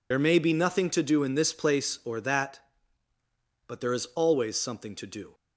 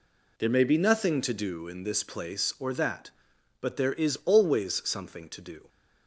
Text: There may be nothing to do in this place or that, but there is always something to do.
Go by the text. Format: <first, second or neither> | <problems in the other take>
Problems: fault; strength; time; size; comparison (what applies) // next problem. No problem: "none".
second | loses the start of "There"; at 0.1 s; 65 ms